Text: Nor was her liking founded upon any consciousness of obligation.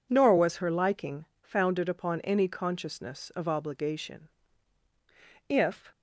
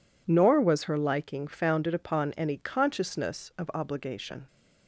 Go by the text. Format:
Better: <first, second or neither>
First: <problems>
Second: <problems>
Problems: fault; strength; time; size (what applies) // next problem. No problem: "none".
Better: second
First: pauses between "liking" and "founded"; slight; at 1.2 s; 0.16 s long // goes on to say "If"; slight; from 5.4 s on; 0.42 s long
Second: none